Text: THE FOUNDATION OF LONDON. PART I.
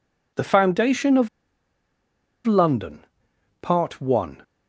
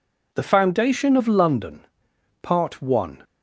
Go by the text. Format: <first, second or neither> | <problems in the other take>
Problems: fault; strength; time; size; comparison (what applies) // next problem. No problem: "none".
second | pauses between "OF" and "LONDON"; at 1.2 s; 1.1 s long